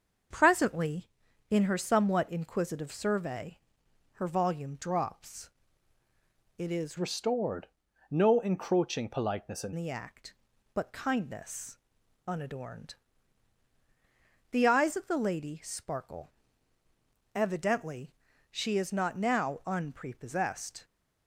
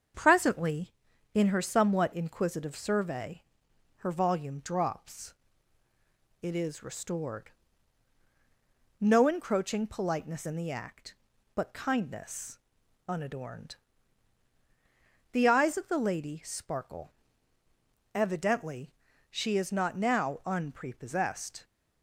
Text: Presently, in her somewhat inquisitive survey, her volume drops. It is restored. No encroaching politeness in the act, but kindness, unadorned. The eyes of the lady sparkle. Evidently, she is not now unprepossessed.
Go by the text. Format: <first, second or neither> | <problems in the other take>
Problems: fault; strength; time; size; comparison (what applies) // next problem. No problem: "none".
second | starts louder than the rest; until 1.7 s; 6 dB; also in the second // changes voice from "restored" to "in"; from 6.9 to 9.7 s; 2.8 s long